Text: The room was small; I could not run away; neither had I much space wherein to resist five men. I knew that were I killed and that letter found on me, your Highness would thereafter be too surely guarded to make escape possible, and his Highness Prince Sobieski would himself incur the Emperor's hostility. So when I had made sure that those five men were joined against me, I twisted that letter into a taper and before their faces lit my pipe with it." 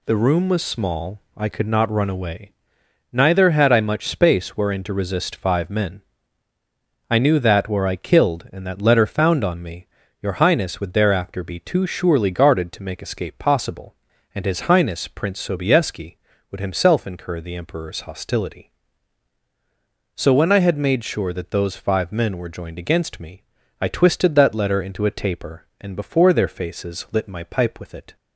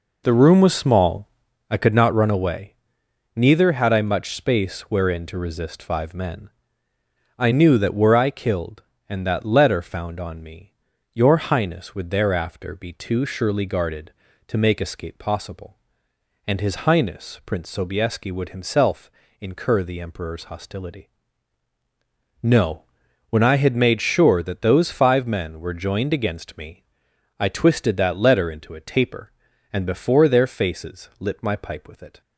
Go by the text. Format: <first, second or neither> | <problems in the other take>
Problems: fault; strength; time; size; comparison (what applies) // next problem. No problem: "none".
first | pauses between "himself" and "incur"; slight; at 19.1 s; 0.30 s long // says "No" for "So"; at 22.4 s